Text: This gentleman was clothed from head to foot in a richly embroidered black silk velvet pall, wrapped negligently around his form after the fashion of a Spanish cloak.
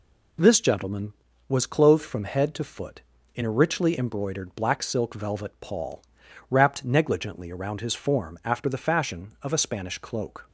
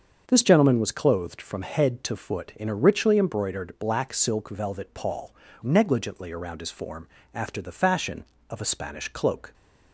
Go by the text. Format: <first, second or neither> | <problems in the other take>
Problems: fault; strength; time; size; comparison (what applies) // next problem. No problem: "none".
first | starts louder than the rest; until 1.2 s; 7 dB // skips "wrapped"; at 5.4 s // pauses between "form" and "after"; slight; at 7.0 s; 0.26 s long